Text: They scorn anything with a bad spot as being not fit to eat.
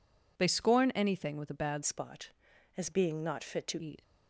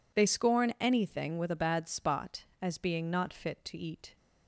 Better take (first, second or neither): second